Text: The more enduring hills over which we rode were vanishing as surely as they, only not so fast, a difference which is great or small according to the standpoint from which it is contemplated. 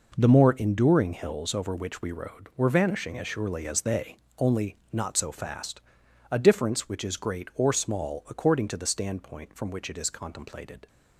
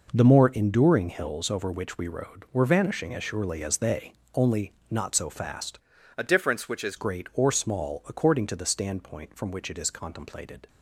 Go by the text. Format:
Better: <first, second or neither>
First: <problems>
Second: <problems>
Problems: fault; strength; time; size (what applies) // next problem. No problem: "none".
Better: first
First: pauses between "only" and "not"; slight; at 4.7 s; 0.16 s long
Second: pauses between "only" and "not"; slight; at 4.7 s; 0.18 s long // changes voice from "a" to "is"; from 6.1 to 6.9 s; 0.8 s long